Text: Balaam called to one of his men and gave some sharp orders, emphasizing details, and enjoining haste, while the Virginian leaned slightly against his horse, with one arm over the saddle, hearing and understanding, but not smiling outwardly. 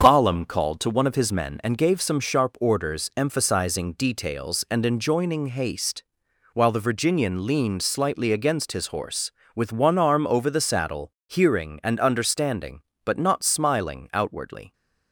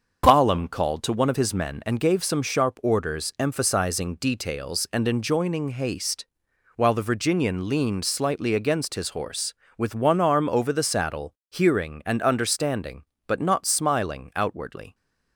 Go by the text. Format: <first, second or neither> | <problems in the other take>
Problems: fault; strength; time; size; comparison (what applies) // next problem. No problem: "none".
neither | starts louder than the rest; the same in both